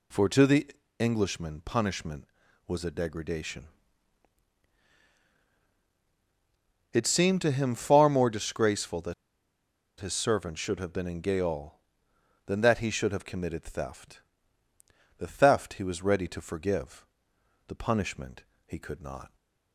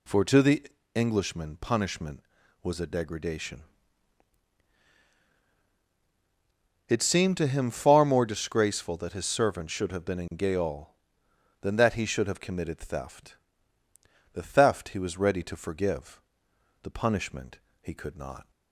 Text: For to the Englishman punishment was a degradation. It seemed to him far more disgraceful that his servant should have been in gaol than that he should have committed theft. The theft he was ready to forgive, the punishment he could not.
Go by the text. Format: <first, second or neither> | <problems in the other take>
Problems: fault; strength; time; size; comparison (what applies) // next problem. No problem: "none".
second | pauses between "the" and "Englishman"; slight; at 0.6 s; 0.30 s long; slight in the second // pauses between "that" and "his"; noticeable; at 9.1 s; 0.84 s long // pauses between "punishment" and "he"; slight; at 18.4 s; 0.20 s long; slight in the second